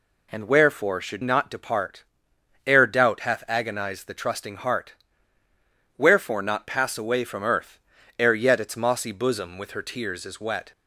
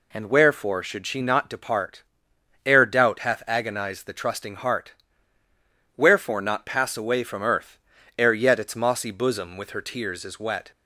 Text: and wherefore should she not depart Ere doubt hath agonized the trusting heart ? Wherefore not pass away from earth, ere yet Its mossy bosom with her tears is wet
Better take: second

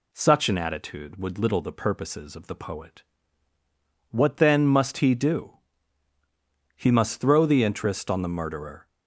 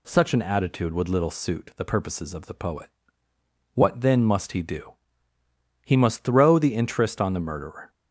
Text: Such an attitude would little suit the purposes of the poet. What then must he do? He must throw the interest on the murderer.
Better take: second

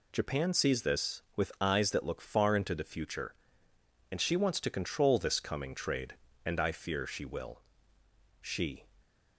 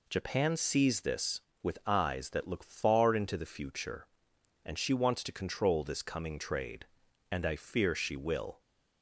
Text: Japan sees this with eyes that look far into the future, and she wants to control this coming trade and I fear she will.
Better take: second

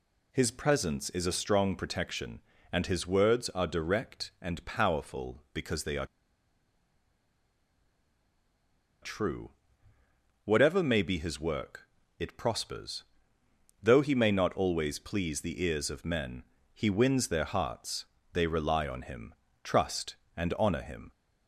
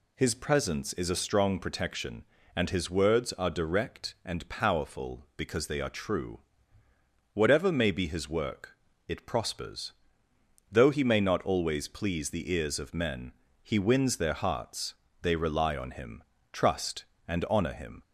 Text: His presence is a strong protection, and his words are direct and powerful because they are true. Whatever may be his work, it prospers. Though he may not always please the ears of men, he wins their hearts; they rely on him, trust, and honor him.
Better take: second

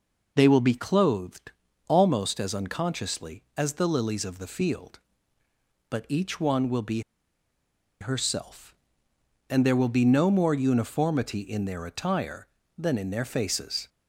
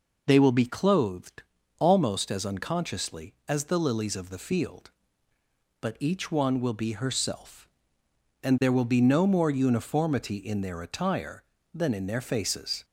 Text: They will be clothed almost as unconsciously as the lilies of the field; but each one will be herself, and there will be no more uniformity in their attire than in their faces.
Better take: second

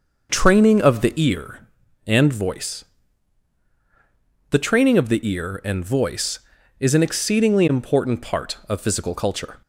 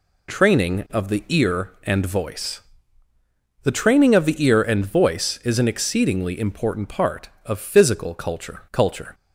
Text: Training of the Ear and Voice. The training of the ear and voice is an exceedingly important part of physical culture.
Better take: first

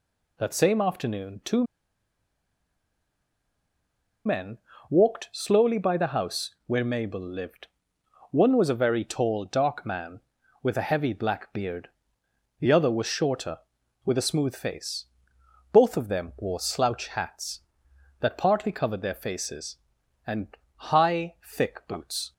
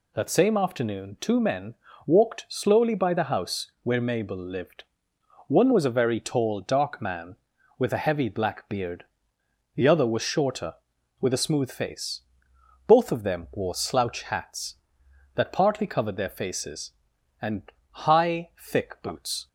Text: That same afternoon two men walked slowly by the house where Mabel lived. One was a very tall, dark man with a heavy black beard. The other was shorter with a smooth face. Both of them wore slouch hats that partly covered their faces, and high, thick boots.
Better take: second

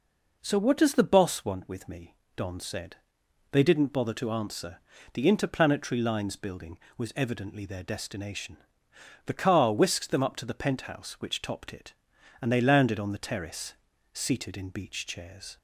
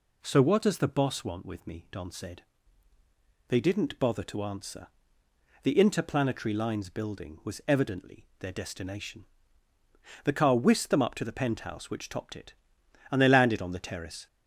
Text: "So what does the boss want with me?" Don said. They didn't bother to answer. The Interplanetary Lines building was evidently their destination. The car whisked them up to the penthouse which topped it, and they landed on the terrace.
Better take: second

